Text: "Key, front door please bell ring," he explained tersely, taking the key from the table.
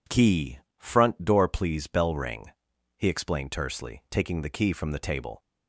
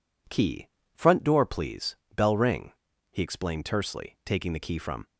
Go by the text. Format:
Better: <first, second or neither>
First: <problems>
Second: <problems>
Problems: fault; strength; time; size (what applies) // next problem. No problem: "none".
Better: first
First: none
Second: pauses between "please" and "bell"; slight; at 1.9 s; 0.20 s long // stops before "the table"; at 5.0 s